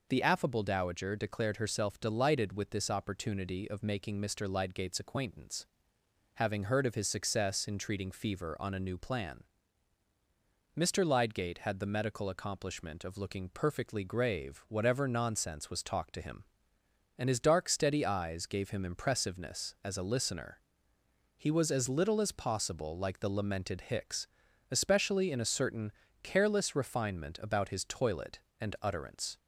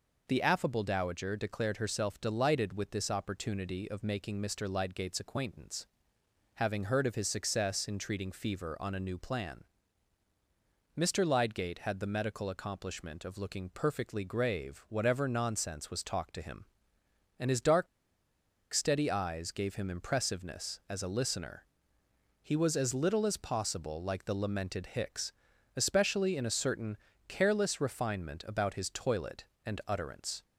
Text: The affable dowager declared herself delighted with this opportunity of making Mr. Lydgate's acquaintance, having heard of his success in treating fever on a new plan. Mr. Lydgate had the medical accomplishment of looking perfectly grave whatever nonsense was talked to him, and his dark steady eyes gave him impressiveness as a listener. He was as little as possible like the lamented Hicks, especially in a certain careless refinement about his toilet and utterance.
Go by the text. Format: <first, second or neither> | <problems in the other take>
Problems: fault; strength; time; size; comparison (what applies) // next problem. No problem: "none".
first | pauses between "dark" and "steady"; noticeable; at 17.8 s; 0.86 s long // pauses between "certain" and "careless"; slight; at 26.9 s; 0.32 s long; slight in the first